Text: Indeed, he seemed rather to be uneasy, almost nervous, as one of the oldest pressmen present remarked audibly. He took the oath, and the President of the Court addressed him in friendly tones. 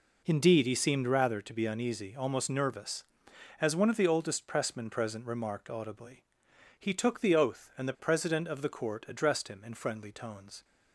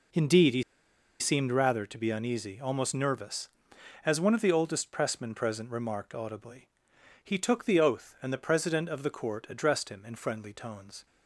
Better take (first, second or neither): first